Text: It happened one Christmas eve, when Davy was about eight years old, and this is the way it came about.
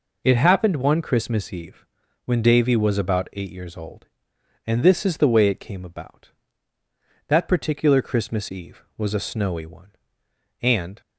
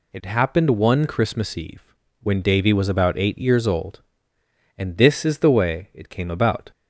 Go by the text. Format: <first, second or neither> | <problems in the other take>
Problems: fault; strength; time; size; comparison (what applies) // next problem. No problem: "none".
second | goes on to say "That particular Christmas eve was a snowy one and"; strong; from 7.2 s on; 3.7 s long